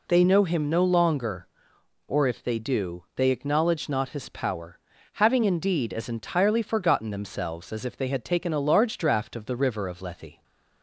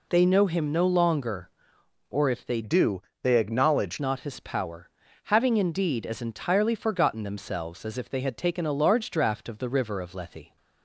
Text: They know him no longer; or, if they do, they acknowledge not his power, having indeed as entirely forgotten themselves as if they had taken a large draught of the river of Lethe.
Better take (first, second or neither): first